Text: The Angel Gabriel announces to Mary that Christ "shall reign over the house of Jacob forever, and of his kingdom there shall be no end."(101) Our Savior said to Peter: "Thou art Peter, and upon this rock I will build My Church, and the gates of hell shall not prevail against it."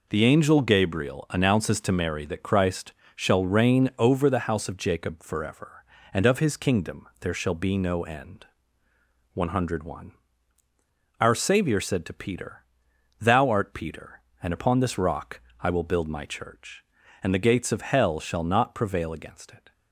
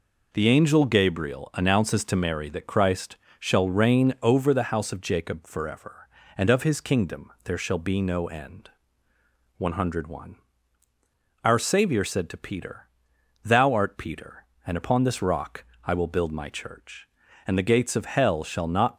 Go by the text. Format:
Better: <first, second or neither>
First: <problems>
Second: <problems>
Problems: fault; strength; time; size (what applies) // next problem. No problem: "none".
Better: first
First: pauses between "Christ" and "shall"; slight; at 2.9 s; 0.24 s long // pauses between "rock" and "I"; slight; at 15.3 s; 0.20 s long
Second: pauses between "Christ" and "shall"; slight; at 3.1 s; 0.24 s long // pauses between "rock" and "I"; slight; at 15.6 s; 0.20 s long // stops before "prevail against it"; at 18.9 s